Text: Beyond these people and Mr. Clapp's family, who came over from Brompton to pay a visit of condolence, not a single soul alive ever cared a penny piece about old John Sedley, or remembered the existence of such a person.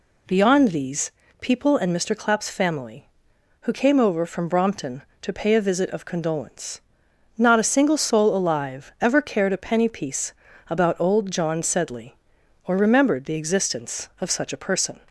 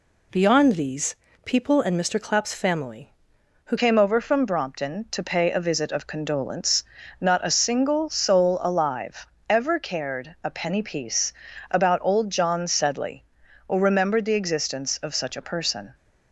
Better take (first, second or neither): first